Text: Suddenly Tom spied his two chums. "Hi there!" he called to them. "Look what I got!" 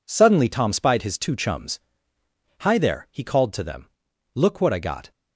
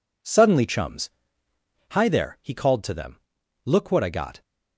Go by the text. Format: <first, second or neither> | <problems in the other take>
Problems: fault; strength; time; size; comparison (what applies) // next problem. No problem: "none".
first | skips "Tom spied his two"; at 0.6 s